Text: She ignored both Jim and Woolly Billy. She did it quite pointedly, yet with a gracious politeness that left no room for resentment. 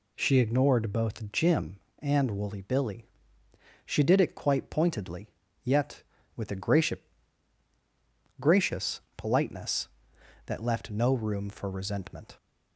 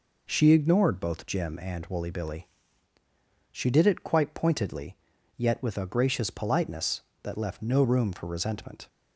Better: second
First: says "gracious" twice; at 8.4 s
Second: none

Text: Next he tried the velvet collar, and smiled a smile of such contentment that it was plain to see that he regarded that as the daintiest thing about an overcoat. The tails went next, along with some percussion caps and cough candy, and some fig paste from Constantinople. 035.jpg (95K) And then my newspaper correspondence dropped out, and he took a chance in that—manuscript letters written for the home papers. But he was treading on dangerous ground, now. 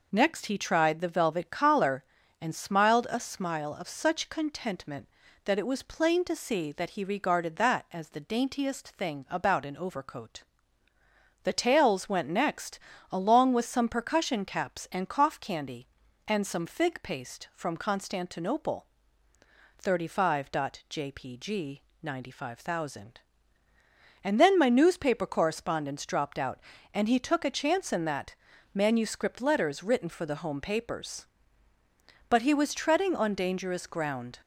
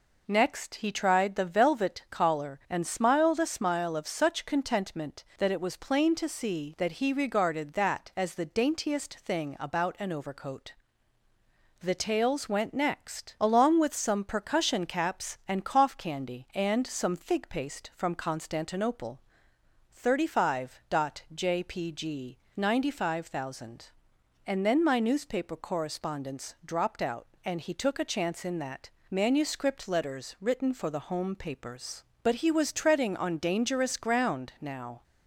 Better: second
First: stops before "now"; at 34.4 s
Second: none

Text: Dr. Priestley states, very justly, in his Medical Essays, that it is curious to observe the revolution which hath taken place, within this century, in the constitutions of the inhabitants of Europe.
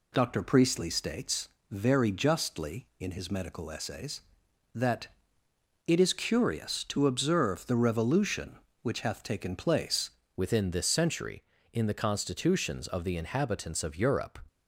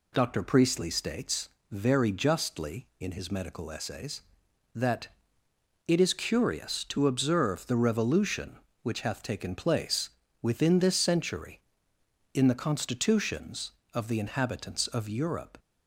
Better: second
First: pauses between "that" and "it"; noticeable; at 5.0 s; 0.80 s long // changes voice at "within"; from 10.3 s on; 4.0 s long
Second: pauses between "that" and "it"; noticeable; at 5.0 s; 0.80 s long

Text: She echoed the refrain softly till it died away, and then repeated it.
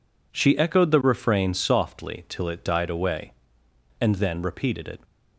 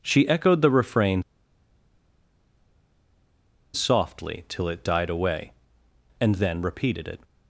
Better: first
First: none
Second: pauses between "refrain" and "softly"; strong; at 1.2 s; 2.5 s long

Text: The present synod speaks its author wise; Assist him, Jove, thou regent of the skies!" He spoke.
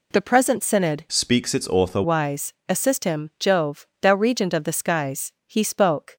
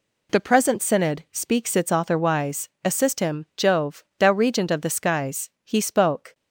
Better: second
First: changes voice from "speaks" to "author"; from 1.0 to 2.0 s; 1.0 s long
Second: none

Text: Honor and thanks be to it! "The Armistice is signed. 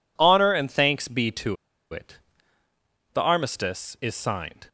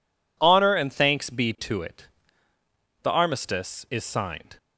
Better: second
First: pauses between "to" and "it"; at 1.5 s; 0.37 s long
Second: none

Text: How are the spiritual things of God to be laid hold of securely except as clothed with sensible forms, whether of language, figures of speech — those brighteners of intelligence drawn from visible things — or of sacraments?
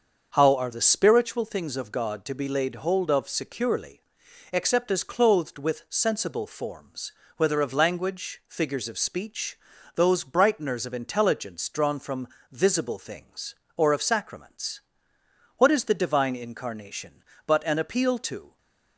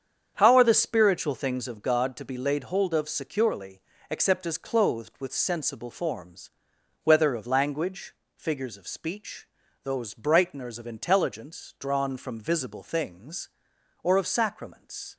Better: second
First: starts louder than the rest; until 1.3 s; 6.5 dB // pauses between "securely" and "except"; noticeable; at 4.0 s; 0.50 s long // pauses between "from" and "visible"; slight; at 12.2 s; 0.20 s long // goes on to say "What is the Divine Incarnation but an appeal to"; strong; from 15.5 s on; 3.0 s long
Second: starts louder than the rest; strong; until 1.3 s; 7.5 dB // pauses between "securely" and "except"; slight; at 3.7 s; 0.30 s long

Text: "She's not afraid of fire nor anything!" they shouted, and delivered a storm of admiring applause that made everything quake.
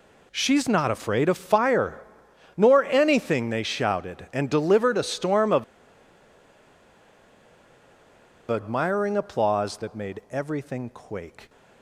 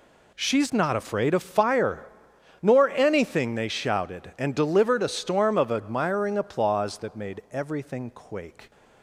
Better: second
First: pauses between "fire" and "nor"; noticeable; at 2.0 s; 0.52 s long // pauses between "of" and "admiring"; strong; at 5.6 s; 2.8 s long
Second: pauses between "fire" and "nor"; noticeable; at 2.0 s; 0.52 s long

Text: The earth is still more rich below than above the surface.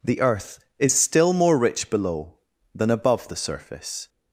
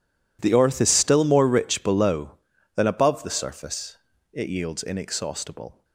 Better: first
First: none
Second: goes on to say "It yields inexhaustible"; from 4.3 s on; 1.5 s long

